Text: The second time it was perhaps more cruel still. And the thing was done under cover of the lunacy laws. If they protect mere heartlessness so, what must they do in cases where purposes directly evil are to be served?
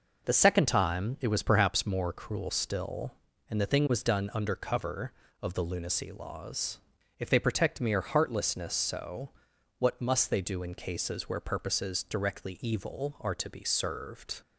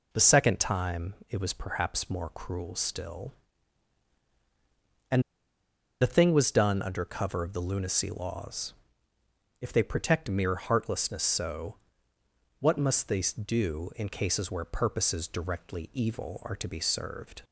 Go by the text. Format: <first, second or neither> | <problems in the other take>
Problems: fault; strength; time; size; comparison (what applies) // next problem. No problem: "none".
first | pauses between "And" and "the"; noticeable; at 5.2 s; 0.79 s long